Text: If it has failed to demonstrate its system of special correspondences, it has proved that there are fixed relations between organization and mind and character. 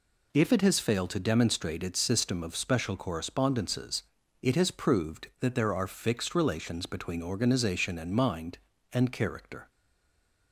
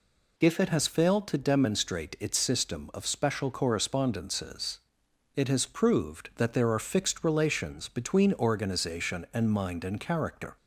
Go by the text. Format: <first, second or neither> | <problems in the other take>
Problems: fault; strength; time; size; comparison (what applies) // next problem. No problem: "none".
second | stays silent after the last word; slight; from 9.6 s on; 0.9 s long